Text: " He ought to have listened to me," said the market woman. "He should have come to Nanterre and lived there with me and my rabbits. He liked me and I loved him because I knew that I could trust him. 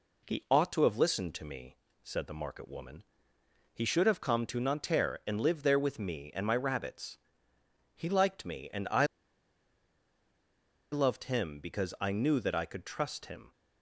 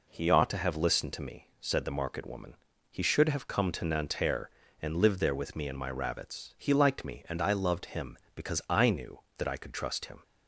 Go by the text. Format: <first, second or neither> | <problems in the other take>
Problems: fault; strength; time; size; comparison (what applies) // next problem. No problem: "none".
second | pauses between "I" and "loved"; strong; at 9.0 s; 1.8 s long